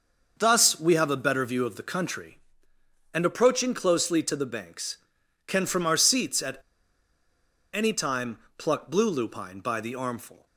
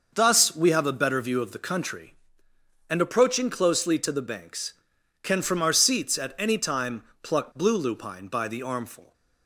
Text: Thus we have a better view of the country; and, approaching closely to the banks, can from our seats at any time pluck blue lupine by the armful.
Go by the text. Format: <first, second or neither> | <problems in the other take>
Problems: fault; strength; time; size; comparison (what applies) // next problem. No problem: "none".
second | starts louder than the rest; noticeable; until 1.3 s; 6 dB // pauses between "at" and "any"; at 6.5 s; 1.1 s long // pauses between "time" and "pluck"; slight; at 8.3 s; 0.20 s long; slight in the second